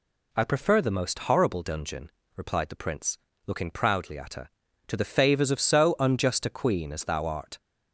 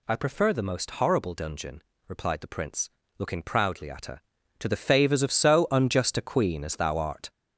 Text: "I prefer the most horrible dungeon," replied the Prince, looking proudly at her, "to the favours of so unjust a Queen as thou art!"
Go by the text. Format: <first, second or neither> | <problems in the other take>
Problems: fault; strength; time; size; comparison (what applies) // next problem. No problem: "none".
first | gets louder; noticeable; throughout; 6 dB